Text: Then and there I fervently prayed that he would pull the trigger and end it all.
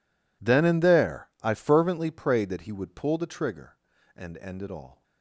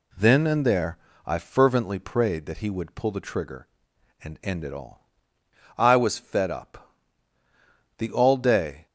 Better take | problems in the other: first | pauses between "there" and "I"; slight; at 0.9 s; 0.28 s long // goes on to say "I was fed up The all day"; strong; from 5.7 s on; 3.0 s long

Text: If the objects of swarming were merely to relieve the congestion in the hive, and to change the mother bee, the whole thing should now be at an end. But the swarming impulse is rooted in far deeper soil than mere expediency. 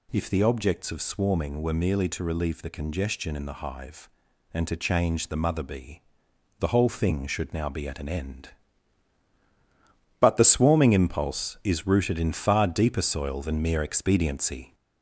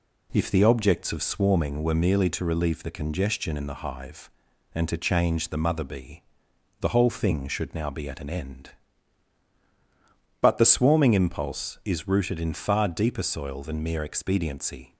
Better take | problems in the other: second | gets louder; slight; throughout; 3 dB

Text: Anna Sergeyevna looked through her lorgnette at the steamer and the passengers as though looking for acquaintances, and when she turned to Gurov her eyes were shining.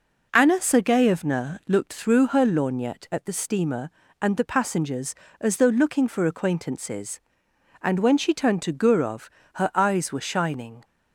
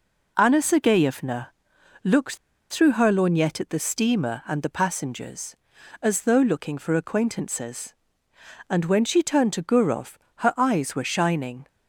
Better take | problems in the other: first | pauses between "Sergeyevna" and "looked"; noticeable; at 1.5 s; 0.50 s long // pauses between "looked" and "through"; slight; at 2.3 s; 0.35 s long // pauses between "Gurov" and "her"; slight; at 10.1 s; 0.20 s long; slight in the first

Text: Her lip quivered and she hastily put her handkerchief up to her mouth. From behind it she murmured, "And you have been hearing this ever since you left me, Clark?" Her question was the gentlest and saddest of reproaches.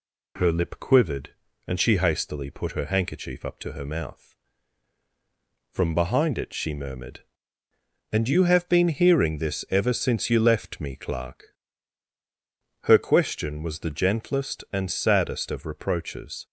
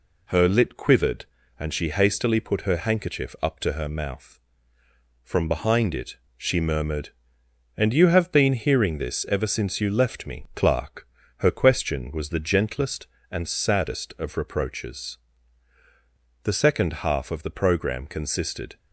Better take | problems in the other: first | pauses between "it" and "she"; slight; at 6.1 s; 0.20 s long // goes on to say "The second half of the program consisted"; strong; from 16.4 s on; 2.3 s long

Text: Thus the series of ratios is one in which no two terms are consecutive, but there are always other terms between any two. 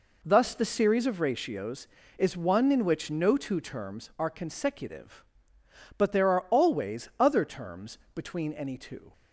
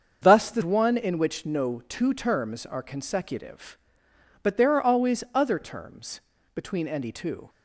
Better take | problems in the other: first | starts louder than the rest; until 1.2 s; 7 dB // skips "series of ratios is"; at 0.6 s // pauses between "terms" and "between"; slight; at 6.2 s; 0.32 s long; slight in the first

